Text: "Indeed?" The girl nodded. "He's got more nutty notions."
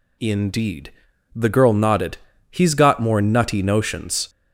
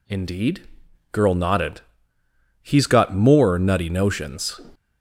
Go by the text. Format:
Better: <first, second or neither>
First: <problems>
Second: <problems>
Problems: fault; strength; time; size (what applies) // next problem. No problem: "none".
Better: first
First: none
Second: skips "The"; at 0.8 s